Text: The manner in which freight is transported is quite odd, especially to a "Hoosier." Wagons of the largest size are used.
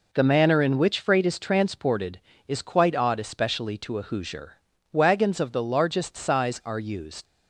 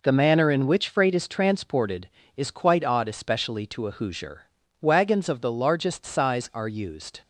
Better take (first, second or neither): second